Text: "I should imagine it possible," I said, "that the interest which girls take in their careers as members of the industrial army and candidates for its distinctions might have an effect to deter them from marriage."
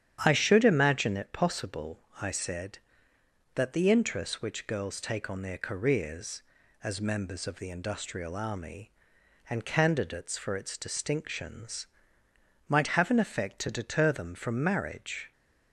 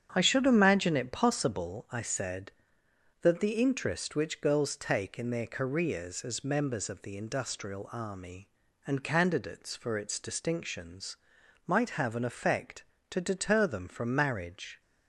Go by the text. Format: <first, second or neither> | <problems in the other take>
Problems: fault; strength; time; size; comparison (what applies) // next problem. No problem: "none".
second | starts louder than the rest; strong; until 1.2 s; 9.5 dB; strong in the second // says "on" for "in"; at 5.2 s // pauses between "distinctions" and "might"; noticeable; at 11.8 s; 0.80 s long; noticeable in the second